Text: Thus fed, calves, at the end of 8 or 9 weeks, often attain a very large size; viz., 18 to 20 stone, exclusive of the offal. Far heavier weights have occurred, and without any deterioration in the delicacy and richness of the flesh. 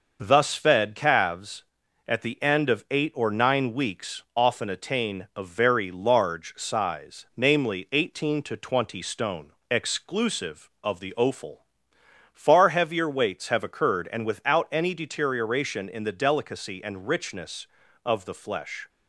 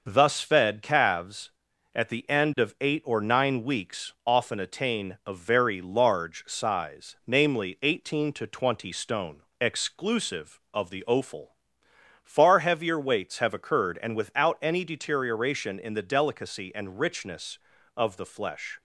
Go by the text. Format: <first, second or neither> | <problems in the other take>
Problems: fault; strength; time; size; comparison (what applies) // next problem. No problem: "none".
neither | none